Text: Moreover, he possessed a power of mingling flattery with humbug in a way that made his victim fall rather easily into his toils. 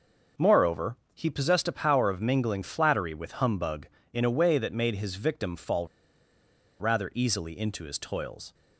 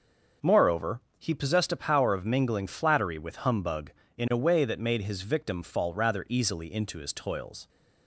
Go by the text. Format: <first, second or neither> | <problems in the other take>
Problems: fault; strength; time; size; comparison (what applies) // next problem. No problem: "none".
second | starts louder than the rest; noticeable; until 1.5 s; 6 dB; also in the second // pauses between "fall" and "rather"; noticeable; at 5.8 s; 0.93 s long